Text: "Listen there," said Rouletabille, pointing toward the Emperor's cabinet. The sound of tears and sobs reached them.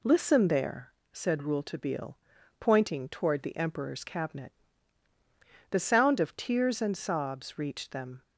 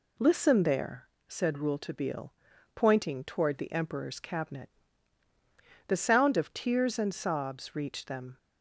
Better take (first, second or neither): neither